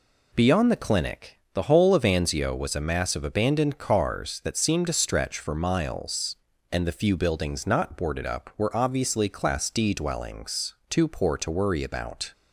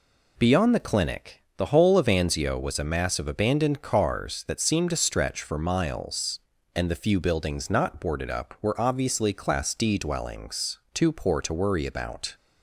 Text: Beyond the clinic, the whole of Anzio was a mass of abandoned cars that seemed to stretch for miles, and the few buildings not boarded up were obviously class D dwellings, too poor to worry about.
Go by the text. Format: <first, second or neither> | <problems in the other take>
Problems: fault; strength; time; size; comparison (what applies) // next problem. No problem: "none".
neither | none